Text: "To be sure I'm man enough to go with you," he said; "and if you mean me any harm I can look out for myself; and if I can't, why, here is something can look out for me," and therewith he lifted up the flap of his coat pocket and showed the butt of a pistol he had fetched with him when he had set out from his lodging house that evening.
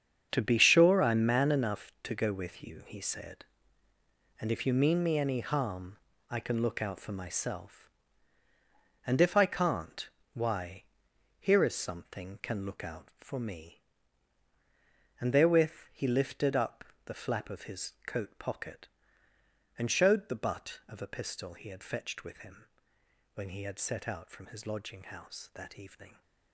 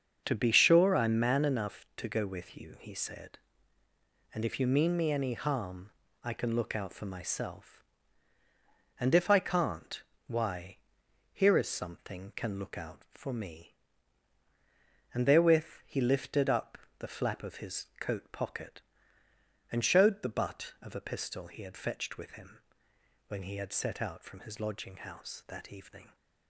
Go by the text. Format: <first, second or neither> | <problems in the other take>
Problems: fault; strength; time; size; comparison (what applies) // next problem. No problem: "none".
second | gets quieter; strong; throughout; 11.5 dB // starts louder than the rest; strong; until 1.3 s; 7.5 dB; also in the second // pauses between "harm" and "I"; slight; at 5.9 s; 0.30 s long; slight in the second // pauses between "up" and "the"; slight; at 16.8 s; 0.22 s long; slight in the second // pauses between "him" and "when"; noticeable; at 22.6 s; 0.66 s long; noticeable in the second